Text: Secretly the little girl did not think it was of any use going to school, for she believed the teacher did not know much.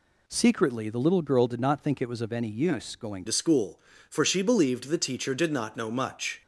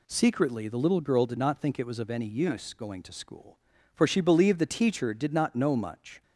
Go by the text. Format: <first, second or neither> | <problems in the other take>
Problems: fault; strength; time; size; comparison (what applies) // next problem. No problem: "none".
second | changes voice at "to"; from 3.2 s on; 3.2 s long